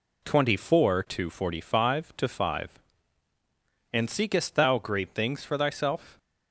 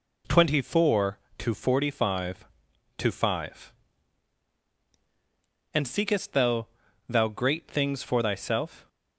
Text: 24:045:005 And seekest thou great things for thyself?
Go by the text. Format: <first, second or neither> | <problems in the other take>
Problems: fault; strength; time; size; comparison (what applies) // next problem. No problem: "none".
first | says "thou" twice; at 7.0 s